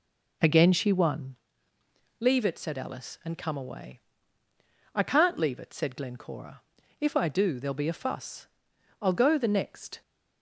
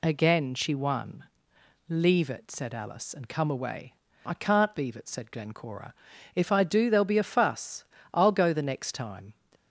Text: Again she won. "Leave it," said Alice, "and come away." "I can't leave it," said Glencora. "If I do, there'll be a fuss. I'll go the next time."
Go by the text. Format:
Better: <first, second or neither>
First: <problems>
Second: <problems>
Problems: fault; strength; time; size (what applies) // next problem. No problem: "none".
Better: second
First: stops before "time"; at 10.0 s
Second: none